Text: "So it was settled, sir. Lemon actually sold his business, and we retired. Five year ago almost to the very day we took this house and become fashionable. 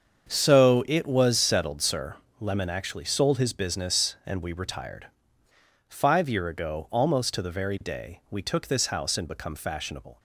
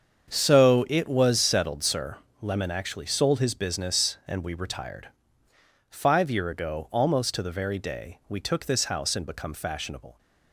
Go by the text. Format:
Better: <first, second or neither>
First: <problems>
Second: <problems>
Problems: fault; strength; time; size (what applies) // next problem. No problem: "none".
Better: neither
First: starts louder than the rest; strong; until 1.3 s; 7 dB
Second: starts louder than the rest; strong; until 1.3 s; 7 dB